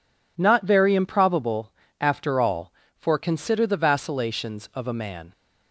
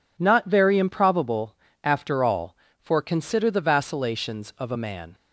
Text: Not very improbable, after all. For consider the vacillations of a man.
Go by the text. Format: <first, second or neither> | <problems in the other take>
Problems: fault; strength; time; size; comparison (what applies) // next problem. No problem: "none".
neither | none